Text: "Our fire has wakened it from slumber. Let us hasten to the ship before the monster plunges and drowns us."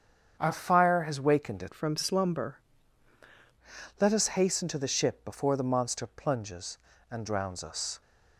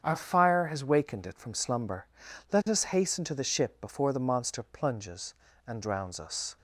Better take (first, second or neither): second